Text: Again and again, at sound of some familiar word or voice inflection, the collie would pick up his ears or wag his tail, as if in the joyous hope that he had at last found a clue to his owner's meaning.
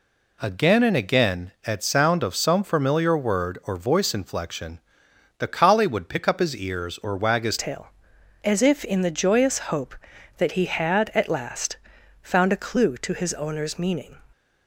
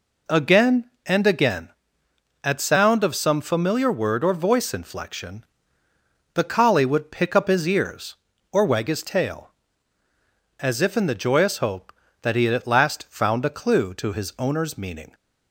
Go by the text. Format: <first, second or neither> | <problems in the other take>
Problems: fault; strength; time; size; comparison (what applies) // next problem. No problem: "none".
second | changes voice at "tail"; from 7.5 s on; 6.6 s long // pauses between "last" and "found"; noticeable; at 11.7 s; 0.46 s long